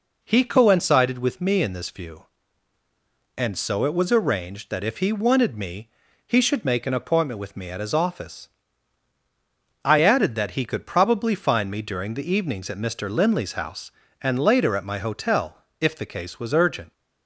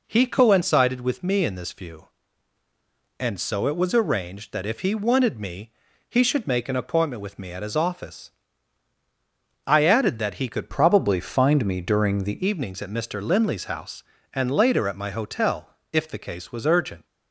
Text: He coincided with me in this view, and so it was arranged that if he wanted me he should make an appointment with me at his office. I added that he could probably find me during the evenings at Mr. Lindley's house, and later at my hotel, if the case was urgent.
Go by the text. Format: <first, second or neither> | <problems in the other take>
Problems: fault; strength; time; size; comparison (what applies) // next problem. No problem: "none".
first | pauses between "me" and "he"; at 5.7 s; 0.38 s long; also in the first // changes voice from "probably" to "the"; from 10.6 to 12.4 s; 1.8 s long